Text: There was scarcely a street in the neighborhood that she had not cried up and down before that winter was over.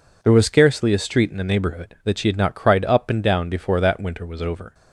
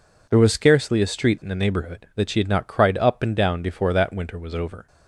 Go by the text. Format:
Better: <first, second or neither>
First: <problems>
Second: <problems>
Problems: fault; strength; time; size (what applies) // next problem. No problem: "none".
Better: neither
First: none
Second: none